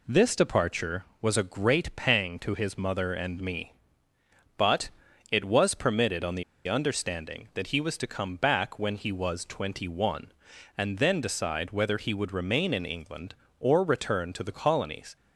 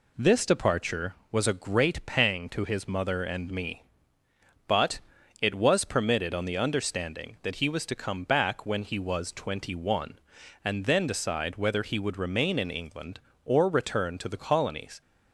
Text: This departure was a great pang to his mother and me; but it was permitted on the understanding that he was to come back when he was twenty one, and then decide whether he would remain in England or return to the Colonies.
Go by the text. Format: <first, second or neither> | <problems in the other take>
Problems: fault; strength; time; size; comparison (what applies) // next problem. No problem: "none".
second | pauses between "but" and "it"; at 4.8 s; 0.42 s long; also in the second // pauses between "the" and "understanding"; slight; at 6.4 s; 0.24 s long